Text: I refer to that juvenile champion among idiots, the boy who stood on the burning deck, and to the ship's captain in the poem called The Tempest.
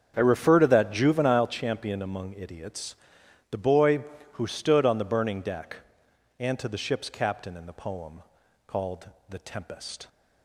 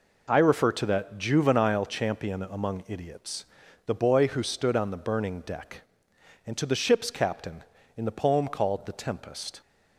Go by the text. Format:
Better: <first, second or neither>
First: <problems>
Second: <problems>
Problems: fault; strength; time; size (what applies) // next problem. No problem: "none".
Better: second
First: starts louder than the rest; until 1.6 s; 7 dB // pauses between "poem" and "called"; at 8.2 s; 0.44 s long // pauses between "called" and "The"; slight; at 9.0 s; 0.20 s long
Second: none